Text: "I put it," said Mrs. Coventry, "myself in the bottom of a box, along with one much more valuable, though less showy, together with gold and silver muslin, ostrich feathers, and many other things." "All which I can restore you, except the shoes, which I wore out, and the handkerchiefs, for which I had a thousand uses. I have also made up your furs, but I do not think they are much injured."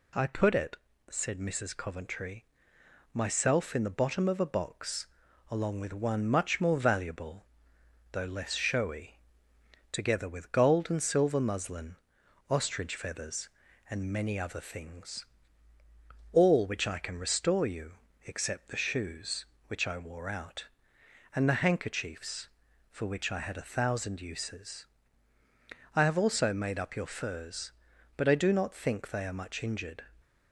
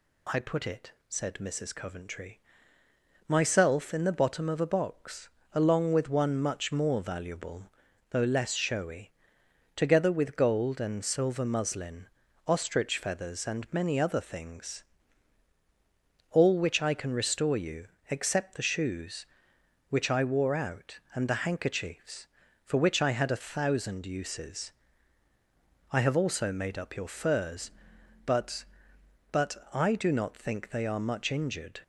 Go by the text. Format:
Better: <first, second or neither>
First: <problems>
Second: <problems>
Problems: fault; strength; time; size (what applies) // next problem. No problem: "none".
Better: first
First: none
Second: says "but" twice; at 29.2 s